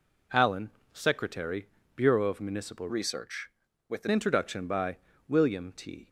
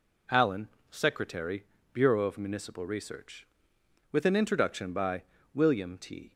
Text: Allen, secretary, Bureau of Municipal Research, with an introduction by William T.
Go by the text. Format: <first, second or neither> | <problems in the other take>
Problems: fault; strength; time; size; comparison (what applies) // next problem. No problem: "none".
second | changes voice from "Research" to "an"; from 2.9 to 4.0 s; 1.1 s long // pauses between "by" and "William"; slight; at 4.9 s; 0.30 s long; slight in the second